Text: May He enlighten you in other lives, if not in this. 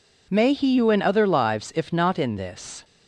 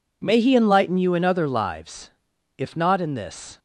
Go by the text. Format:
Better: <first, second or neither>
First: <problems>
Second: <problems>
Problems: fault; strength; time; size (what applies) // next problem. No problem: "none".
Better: second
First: skips "enlighten"; at 0.7 s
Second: none